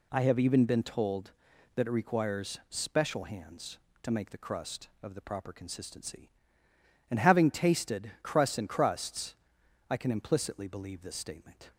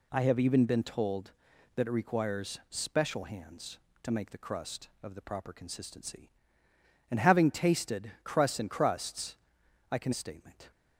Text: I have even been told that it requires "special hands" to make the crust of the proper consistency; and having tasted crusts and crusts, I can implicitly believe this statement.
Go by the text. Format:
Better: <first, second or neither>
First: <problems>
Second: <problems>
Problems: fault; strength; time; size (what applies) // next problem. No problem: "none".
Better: first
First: none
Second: skips "implicitly believe this"; at 10.1 s